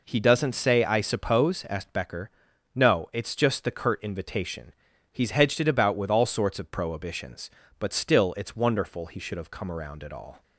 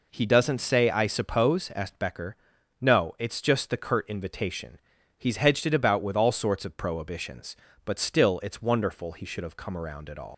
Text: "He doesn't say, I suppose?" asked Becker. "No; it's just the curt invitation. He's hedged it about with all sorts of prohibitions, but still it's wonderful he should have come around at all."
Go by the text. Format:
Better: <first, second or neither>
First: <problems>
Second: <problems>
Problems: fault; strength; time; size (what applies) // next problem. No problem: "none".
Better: first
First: none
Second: leaves "all" unfinished; at 10.3 s; 140 ms